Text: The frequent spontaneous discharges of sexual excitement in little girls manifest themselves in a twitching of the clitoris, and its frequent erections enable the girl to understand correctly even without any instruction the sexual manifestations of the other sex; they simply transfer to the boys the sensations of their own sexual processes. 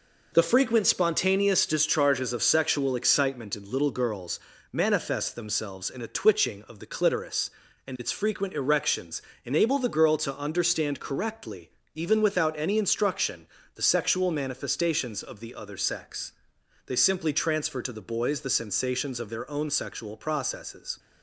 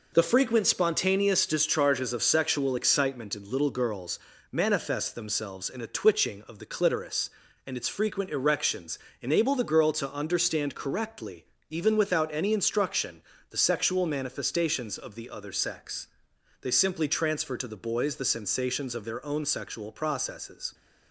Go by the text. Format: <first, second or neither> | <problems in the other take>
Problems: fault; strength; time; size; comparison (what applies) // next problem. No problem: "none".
neither | pauses between "girls" and "manifest"; slight; the same in both // pauses between "erections" and "enable"; slight; the same in both // pauses between "correctly" and "even"; slight; the same in both // pauses between "instruction" and "the"; slight; the same in both